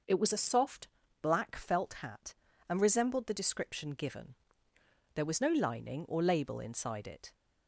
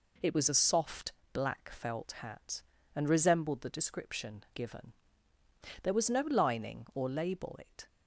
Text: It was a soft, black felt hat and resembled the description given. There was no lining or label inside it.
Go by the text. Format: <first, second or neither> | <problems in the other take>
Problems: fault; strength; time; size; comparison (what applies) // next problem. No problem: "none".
first | skips "inside"; at 7.5 s